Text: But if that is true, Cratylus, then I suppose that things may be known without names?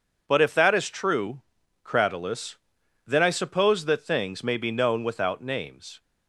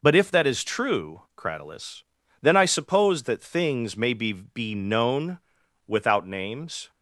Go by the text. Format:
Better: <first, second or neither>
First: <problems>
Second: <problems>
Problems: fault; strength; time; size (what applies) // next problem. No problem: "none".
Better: first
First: none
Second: says "be" twice; at 4.3 s // pauses between "known" and "without"; noticeable; at 5.3 s; 0.48 s long